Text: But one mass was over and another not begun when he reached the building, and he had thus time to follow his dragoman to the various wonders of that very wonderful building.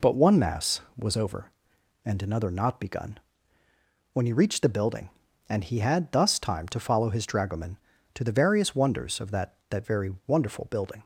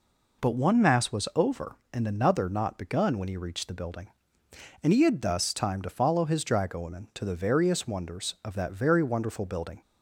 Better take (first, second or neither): second